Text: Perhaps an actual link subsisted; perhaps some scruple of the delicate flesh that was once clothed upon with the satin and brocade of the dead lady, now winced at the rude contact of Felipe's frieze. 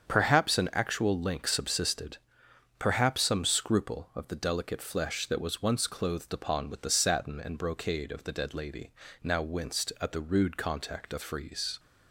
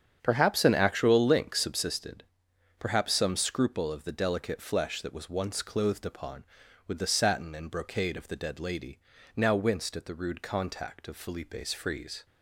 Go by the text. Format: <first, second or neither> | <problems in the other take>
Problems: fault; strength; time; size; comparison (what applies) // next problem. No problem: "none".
second | starts louder than the rest; strong; until 1.1 s; 7 dB; strong in the second // skips "Felipe's"; at 11.2 s